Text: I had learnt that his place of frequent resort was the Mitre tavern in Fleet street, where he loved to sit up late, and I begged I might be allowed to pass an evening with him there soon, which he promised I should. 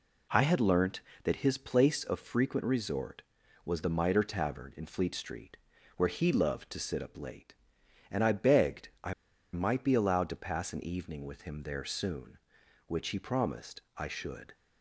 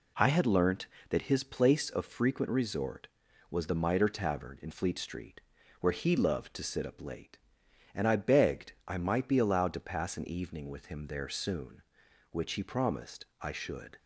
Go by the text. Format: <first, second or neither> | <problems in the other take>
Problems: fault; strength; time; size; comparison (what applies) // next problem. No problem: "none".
second | pauses between "begged" and "I"; slight; at 8.8 s; 0.16 s long; slight in the second // pauses between "I" and "might"; at 9.1 s; 0.40 s long